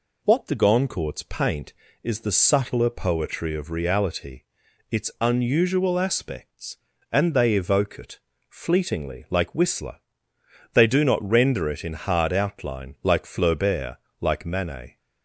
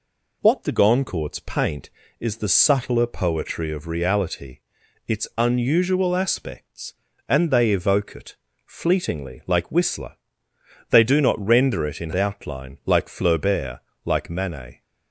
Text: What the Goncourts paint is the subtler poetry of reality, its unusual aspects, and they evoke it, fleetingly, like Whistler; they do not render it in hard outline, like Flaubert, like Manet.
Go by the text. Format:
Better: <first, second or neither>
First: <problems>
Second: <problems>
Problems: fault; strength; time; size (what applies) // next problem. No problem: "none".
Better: first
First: none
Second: skips "hard"; at 12.1 s